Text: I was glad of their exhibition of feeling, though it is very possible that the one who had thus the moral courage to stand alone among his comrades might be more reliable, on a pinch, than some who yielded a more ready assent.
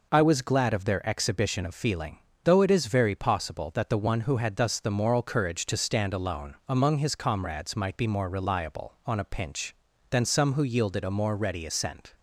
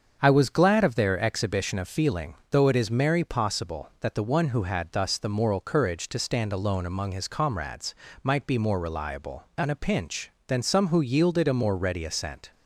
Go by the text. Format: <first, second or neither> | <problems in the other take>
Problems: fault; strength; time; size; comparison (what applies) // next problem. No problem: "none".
first | starts louder than the rest; until 1.2 s; 7 dB // says "merry" for "very"; at 2.9 s // pauses between "comrades" and "might"; slight; at 7.9 s; 0.26 s long